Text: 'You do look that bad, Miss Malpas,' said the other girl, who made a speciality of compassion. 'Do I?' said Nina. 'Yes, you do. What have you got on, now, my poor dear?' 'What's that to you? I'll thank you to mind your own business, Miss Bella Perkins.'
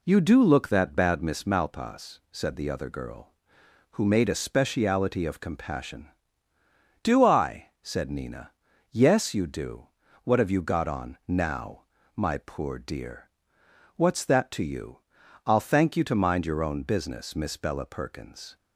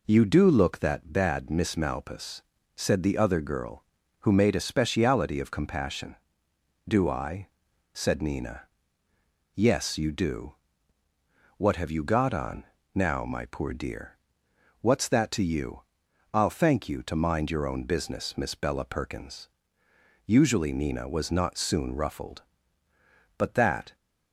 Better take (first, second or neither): first